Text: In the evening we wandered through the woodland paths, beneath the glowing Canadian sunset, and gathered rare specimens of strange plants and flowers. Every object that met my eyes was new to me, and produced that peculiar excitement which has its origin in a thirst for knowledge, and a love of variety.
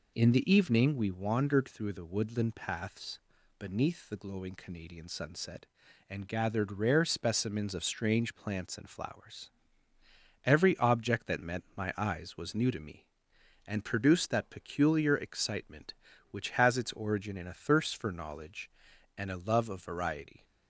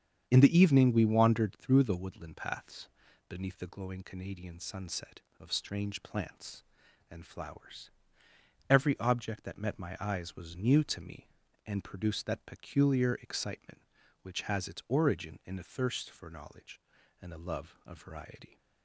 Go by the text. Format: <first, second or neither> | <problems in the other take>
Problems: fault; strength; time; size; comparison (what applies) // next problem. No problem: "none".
first | starts louder than the rest; strong; until 1.2 s; 8 dB // skips "and gathered rare specimens"; at 5.2 s